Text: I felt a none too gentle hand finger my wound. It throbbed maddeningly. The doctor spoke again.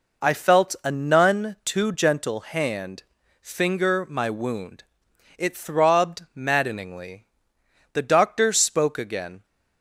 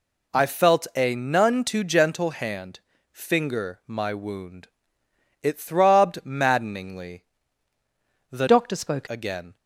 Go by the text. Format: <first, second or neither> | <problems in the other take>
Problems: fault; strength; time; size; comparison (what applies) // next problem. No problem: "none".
first | pauses between "hand" and "finger"; slight; at 2.7 s; 0.32 s long; also in the first // changes voice from "doctor" to "spoke"; from 8.4 to 9.0 s; 0.6 s long